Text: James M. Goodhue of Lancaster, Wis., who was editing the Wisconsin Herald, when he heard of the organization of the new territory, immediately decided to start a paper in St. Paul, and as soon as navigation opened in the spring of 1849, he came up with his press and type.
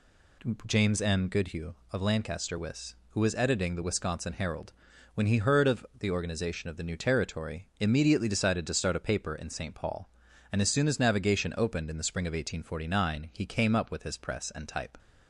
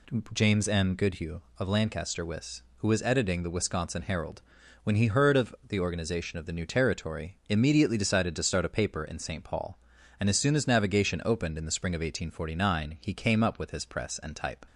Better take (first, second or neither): neither